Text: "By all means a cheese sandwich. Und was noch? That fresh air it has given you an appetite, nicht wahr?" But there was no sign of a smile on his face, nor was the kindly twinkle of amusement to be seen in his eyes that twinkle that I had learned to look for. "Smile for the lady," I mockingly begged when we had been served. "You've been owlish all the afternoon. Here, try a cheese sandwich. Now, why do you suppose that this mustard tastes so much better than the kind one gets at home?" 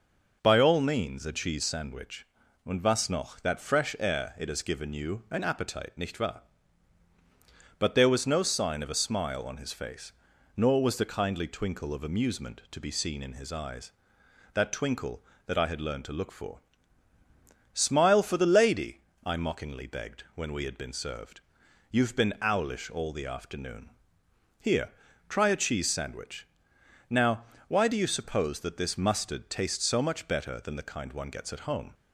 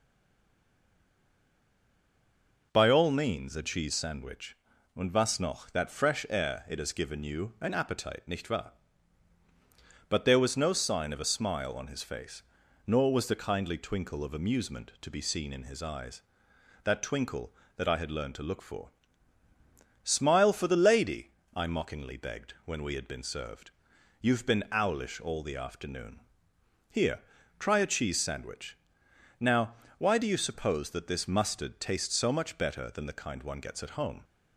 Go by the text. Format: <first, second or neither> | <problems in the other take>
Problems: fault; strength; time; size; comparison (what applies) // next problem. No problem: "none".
first | stays silent before the first word; strong; until 2.7 s; 2.7 s long